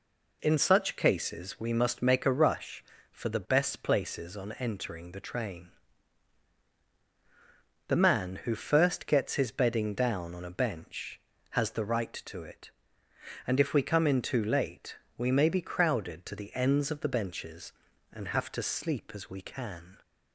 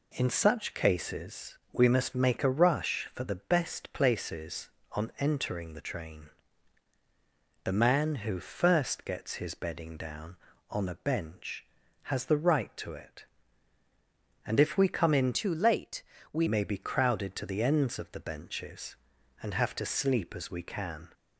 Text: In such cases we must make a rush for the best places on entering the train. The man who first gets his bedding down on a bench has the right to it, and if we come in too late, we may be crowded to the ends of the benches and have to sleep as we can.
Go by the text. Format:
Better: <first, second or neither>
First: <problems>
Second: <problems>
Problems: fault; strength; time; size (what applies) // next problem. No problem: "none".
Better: first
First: none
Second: pauses between "cases" and "we"; slight; at 1.5 s; 0.16 s long // changes voice from "too" to "we"; from 15.3 to 16.4 s; 1.1 s long